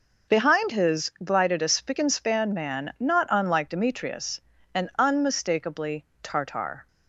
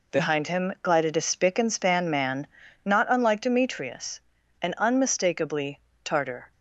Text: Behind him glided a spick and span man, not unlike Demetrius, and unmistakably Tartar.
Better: second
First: says "his" for "him"; at 0.7 s // pauses between "unmistakably" and "Tartar"; slight; at 6.0 s; 0.20 s long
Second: pauses between "unmistakably" and "Tartar"; slight; at 5.7 s; 0.24 s long

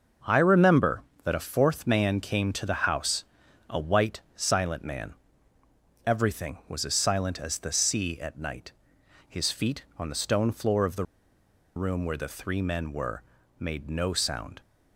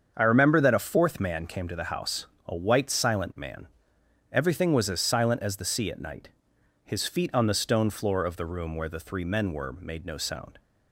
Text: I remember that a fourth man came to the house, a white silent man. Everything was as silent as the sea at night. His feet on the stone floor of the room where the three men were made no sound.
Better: second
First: starts louder than the rest; noticeable; until 1.4 s; 6 dB // pauses between "white" and "silent"; slight; at 4.1 s; 0.16 s long // pauses between "the" and "room"; noticeable; at 11.0 s; 0.71 s long // pauses between "were" and "made"; slight; at 13.2 s; 0.36 s long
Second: starts louder than the rest; strong; until 1.1 s; 7 dB

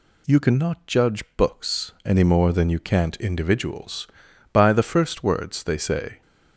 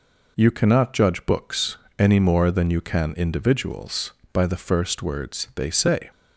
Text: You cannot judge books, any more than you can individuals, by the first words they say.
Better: second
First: says "can't" for "can"; at 2.7 s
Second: none

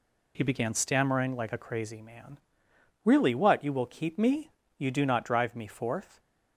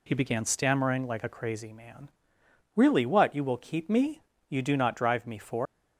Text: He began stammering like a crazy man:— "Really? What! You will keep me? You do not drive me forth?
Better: first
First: none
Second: leaves "forth" unfinished; at 5.6 s; 260 ms

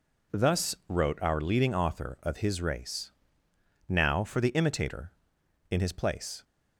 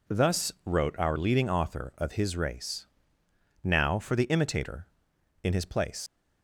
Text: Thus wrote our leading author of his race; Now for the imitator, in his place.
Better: first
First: none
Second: leaves "place" unfinished; at 6.0 s; 95 ms

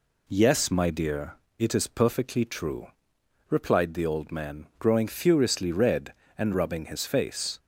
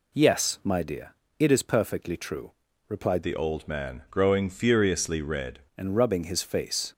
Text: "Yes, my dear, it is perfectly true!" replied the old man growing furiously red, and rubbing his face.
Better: first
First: none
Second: changes voice from "the" to "red"; from 3.2 to 5.5 s; 2.3 s long

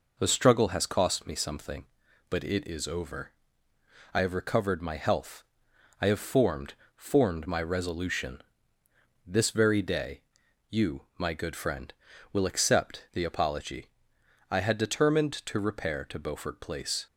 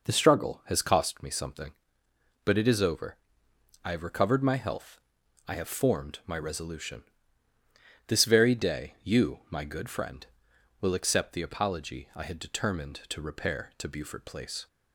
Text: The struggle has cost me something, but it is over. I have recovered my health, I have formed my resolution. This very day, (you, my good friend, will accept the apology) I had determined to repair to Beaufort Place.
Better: second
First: says "formed" twice; at 6.9 s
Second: none

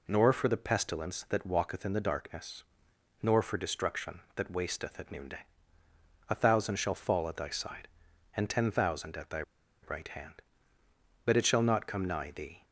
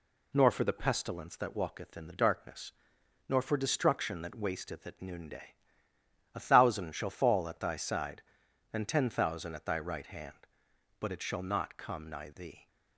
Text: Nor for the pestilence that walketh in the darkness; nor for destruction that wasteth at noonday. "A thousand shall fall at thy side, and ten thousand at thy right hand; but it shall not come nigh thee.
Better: second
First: pauses between "thy" and "right"; at 9.4 s; 0.41 s long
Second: none

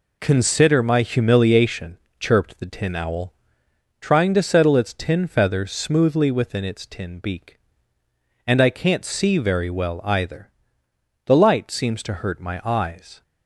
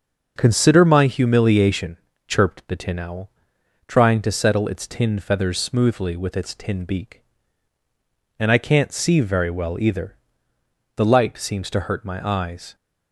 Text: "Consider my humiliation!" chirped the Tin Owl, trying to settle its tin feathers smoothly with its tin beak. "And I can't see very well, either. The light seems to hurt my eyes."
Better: second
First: says "within" for "with"; at 6.3 s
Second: none

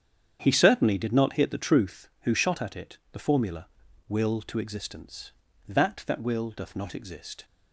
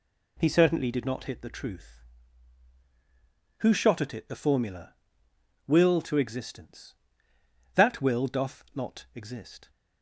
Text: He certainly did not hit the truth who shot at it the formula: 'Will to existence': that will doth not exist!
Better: second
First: starts louder than the rest; strong; until 1.4 s; 8 dB // pauses between "it" and "the"; slight; at 2.9 s; 0.16 s long // says "that" twice; at 6.0 s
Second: none

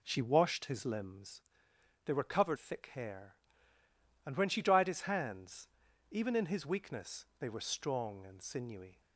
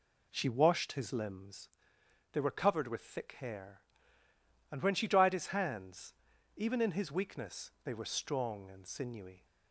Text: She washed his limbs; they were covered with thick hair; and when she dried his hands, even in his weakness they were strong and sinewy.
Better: second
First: skips "with"; at 2.5 s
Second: none

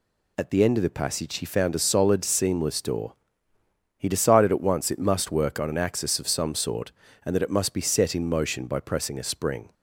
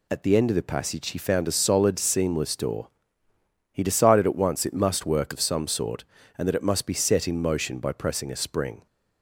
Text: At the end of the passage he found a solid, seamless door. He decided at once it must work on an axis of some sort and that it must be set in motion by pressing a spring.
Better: first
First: none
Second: skips "on an axis"; at 5.3 s

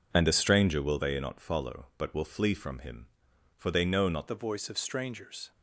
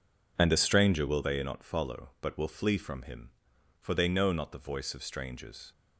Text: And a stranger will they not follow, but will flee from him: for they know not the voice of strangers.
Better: second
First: changes voice at "the"; from 4.2 s on; 1.3 s long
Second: none

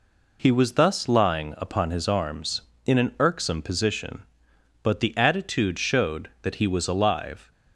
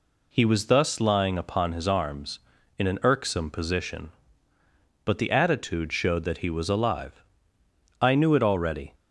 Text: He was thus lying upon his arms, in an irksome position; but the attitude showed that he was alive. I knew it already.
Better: second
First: stops before "I knew it already"; at 7.5 s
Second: none

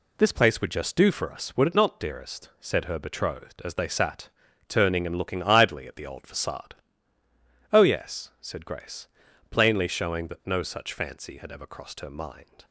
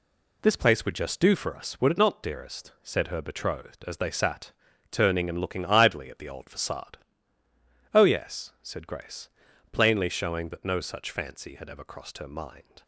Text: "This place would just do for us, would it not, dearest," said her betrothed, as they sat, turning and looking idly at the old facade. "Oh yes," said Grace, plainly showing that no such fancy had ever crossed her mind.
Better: neither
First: none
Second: none

